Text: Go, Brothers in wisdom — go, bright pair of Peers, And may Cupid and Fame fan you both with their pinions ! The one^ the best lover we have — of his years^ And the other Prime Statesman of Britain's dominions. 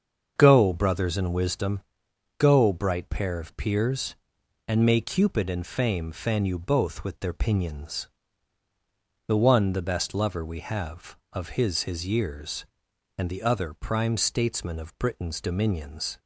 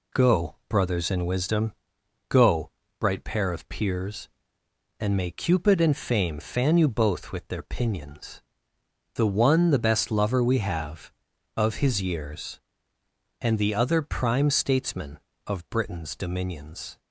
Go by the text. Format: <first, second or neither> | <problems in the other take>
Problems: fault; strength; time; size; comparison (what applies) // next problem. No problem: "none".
second | starts louder than the rest; until 1.3 s; 6.5 dB // says "his" twice; at 11.8 s